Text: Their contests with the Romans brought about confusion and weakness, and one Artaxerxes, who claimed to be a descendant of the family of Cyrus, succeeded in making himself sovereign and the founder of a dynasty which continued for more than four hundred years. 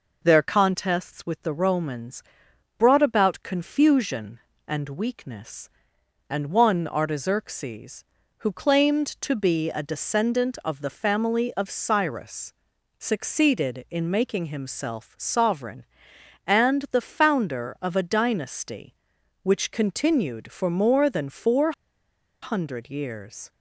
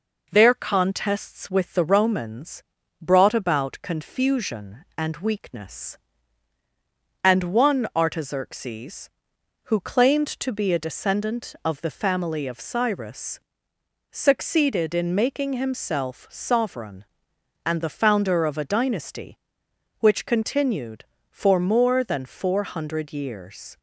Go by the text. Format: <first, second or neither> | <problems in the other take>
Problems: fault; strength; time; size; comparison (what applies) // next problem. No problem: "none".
second | pauses between "Romans" and "brought"; noticeable; at 2.2 s; 0.56 s long; also in the second // pauses between "four" and "hundred"; noticeable; at 21.7 s; 0.69 s long